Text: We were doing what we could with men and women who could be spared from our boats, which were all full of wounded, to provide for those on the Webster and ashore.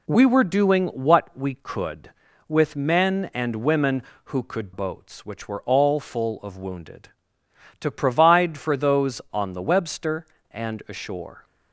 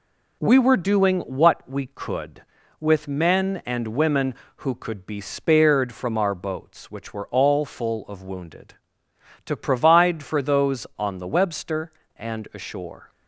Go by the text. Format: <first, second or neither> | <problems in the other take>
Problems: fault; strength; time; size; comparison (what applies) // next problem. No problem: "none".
second | skips "be spared from our"; at 4.7 s